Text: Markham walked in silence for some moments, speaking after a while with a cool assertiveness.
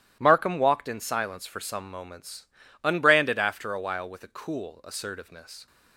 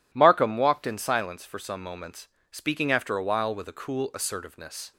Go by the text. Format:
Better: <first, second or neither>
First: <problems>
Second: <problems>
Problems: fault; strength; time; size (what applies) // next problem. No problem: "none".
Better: second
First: starts louder than the rest; strong; until 1.2 s; 13 dB // says "unbranded" for "speaking"; at 2.8 s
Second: none